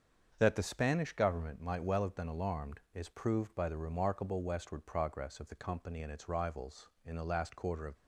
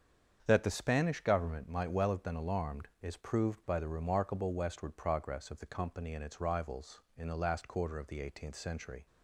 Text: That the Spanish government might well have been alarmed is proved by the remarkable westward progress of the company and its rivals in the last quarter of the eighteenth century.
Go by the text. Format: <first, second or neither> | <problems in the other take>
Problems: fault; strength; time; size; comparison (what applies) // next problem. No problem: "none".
second | starts louder than the rest; until 1.3 s; 7 dB; strong in the second // stops before "the eighteenth century"; at 7.9 s